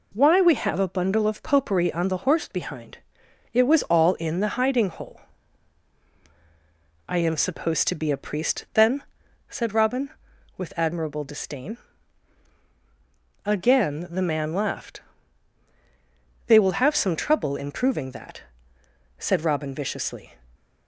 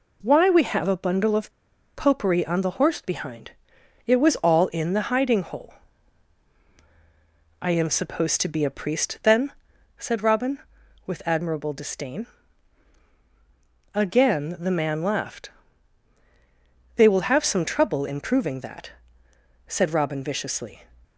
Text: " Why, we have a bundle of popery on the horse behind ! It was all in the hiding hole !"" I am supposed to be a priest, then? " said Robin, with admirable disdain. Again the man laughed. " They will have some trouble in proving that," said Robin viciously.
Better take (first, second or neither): first